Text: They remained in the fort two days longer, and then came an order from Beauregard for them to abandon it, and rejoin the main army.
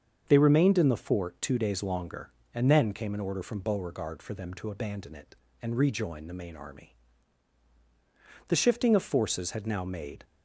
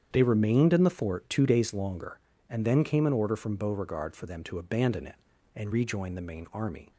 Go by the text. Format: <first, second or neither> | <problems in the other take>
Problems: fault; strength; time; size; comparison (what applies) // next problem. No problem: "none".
second | starts louder than the rest; until 1.2 s; 7 dB; strong in the second // goes on to say "The shifting of forces had now made"; strong; from 8.4 s on; 1.7 s long